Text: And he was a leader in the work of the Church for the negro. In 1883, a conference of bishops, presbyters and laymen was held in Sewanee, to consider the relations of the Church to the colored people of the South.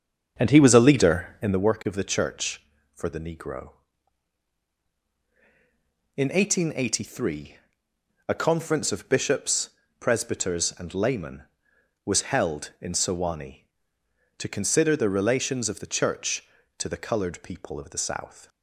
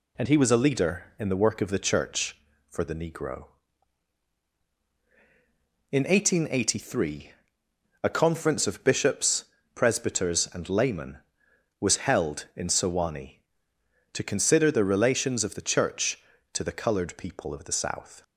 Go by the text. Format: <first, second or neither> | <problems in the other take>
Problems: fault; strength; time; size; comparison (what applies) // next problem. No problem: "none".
second | starts louder than the rest; until 1.7 s; 7 dB